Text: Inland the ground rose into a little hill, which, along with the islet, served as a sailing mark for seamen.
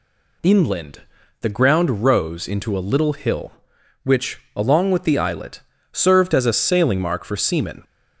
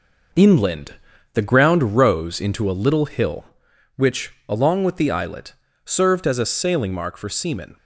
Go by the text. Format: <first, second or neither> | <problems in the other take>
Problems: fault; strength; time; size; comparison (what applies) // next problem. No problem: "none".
first | gets quieter; noticeable; throughout; 5.5 dB // pauses between "Inland" and "the"; at 0.9 s; 0.40 s long; also in the first